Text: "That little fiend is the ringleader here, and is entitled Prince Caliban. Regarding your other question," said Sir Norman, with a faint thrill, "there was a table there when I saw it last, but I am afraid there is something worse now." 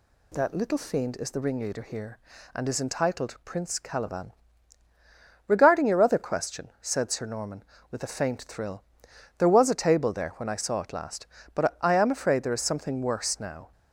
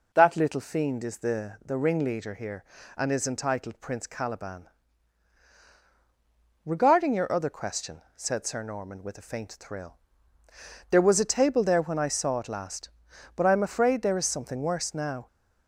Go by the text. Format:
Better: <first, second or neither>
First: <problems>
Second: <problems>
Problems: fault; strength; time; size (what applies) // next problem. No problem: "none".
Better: first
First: none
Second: says "the" twice; at 1.6 s